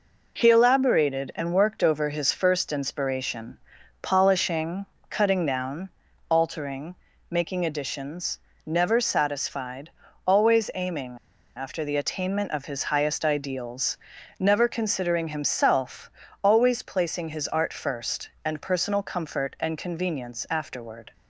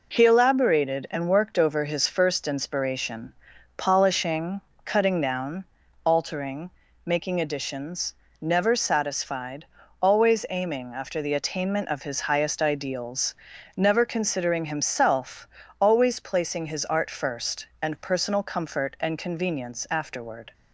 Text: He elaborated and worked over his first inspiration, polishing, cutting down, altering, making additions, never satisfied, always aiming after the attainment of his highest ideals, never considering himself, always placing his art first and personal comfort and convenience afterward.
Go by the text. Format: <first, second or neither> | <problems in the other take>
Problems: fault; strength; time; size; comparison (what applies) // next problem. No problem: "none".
second | pauses between "aiming" and "after"; at 11.1 s; 0.38 s long